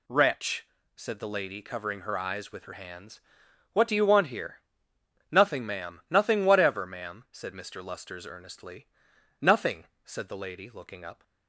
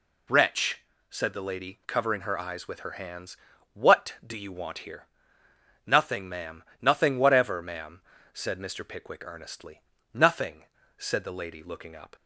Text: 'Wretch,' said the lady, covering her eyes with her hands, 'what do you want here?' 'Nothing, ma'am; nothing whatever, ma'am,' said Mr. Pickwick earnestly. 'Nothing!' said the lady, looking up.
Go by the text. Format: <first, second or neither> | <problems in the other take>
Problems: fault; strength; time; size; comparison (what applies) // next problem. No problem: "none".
second | says "Lusters" for "Pickwick"; at 7.8 s